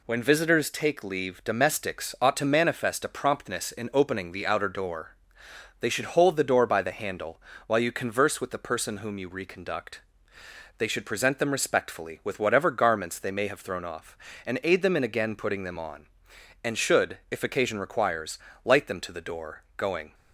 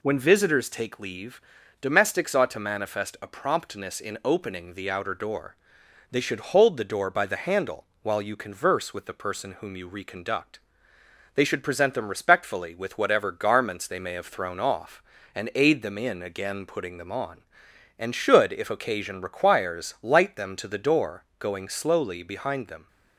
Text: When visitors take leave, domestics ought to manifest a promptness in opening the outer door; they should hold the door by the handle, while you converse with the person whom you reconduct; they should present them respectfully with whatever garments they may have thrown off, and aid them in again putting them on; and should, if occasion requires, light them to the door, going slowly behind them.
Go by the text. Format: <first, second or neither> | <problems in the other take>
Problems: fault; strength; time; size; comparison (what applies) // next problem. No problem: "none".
second | stops before "slowly behind them"; at 20.1 s